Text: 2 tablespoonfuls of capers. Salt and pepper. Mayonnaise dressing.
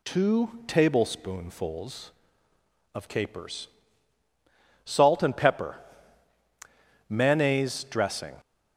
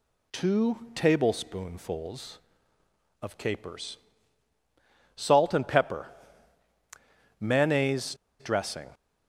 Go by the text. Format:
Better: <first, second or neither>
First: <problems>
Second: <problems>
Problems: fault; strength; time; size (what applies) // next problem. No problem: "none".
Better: first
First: none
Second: pauses between "Mayonnaise" and "dressing"; slight; at 8.1 s; 0.25 s long